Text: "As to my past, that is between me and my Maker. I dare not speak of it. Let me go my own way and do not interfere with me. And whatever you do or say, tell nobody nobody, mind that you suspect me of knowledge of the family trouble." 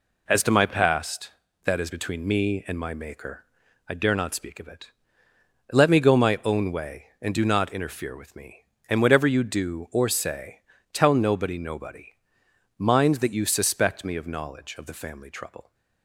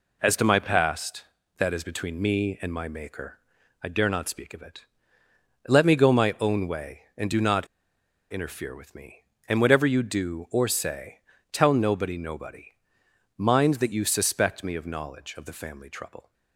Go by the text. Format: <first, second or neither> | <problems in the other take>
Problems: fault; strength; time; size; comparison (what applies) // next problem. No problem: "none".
first | pauses between "not" and "interfere"; noticeable; at 7.6 s; 0.65 s long